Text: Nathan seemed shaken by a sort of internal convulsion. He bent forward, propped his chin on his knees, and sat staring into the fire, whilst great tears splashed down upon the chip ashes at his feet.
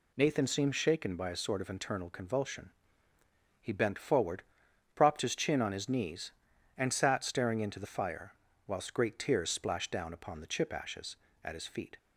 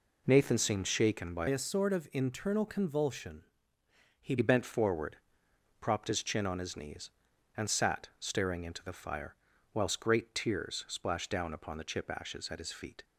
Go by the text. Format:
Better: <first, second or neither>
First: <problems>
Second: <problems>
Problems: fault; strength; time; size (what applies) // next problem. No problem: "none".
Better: first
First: none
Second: changes voice from "a" to "He"; from 1.4 to 4.3 s; 2.9 s long